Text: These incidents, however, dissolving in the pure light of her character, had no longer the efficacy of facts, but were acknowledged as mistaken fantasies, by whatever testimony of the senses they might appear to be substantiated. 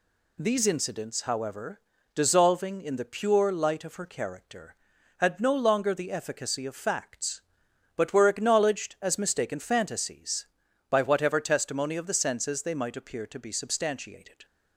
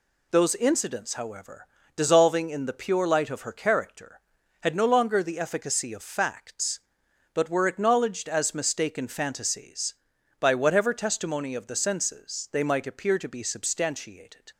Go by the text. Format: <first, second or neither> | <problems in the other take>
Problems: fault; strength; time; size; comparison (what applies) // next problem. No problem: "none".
first | says "Those" for "These"; at 0.3 s